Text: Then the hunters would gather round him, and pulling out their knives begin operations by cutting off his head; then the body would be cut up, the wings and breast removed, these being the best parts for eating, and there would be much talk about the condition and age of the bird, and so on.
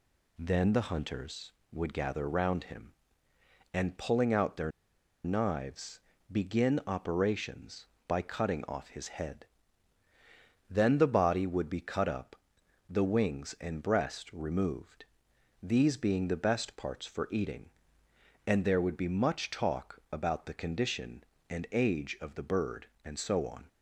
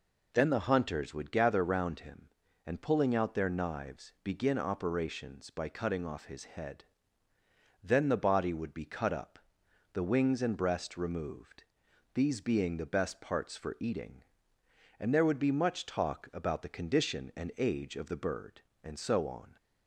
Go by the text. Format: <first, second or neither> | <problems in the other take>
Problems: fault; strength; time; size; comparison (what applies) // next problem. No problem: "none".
second | pauses between "their" and "knives"; noticeable; at 4.7 s; 0.54 s long // pauses between "knives" and "begin"; slight; at 5.9 s; 0.32 s long